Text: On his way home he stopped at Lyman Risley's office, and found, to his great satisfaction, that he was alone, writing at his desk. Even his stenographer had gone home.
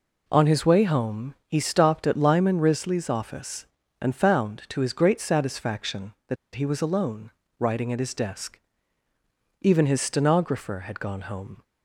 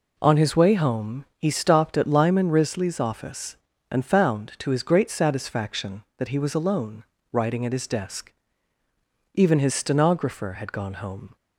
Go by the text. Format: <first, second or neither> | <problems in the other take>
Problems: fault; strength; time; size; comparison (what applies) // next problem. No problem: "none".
second | pauses between "that" and "he"; slight; at 6.3 s; 0.19 s long